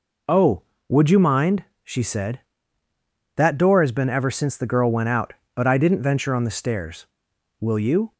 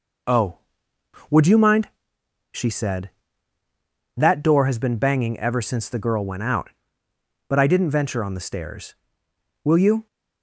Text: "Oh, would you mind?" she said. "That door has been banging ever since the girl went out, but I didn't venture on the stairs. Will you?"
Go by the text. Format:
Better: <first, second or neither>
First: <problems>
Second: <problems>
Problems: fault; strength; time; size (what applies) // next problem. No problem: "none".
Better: second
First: skips "banging"; at 4.0 s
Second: none